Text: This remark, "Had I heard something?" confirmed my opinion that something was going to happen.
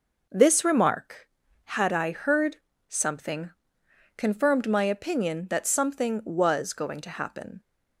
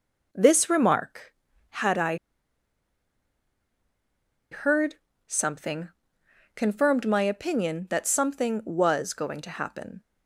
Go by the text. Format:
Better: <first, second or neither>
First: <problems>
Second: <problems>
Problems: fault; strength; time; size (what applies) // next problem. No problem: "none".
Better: first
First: pauses between "heard" and "something"; slight; at 2.5 s; 0.32 s long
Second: pauses between "I" and "heard"; strong; at 2.1 s; 2.3 s long // pauses between "heard" and "something"; slight; at 4.9 s; 0.32 s long